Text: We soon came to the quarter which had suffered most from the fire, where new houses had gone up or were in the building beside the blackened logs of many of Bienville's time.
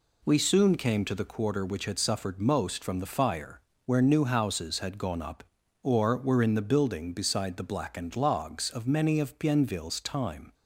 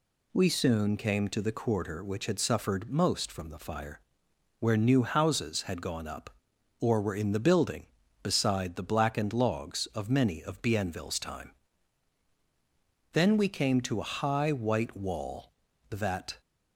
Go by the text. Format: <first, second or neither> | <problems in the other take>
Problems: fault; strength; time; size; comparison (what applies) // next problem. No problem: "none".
first | goes on to say "Then we came to a high white wall that"; strong; from 13.1 s on; 3.2 s long